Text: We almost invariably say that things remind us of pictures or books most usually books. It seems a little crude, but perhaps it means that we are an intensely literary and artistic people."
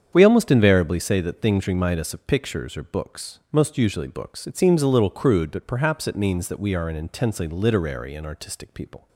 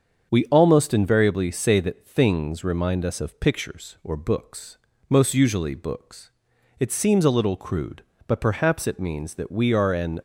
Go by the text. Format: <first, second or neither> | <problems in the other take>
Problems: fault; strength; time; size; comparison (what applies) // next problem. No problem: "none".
first | starts louder than the rest; strong; until 1.3 s; 7 dB; strong in the first // pauses between "books" and "most"; slight; at 4.7 s; 0.34 s long // stops before "intensely literary and artistic people"; at 10.1 s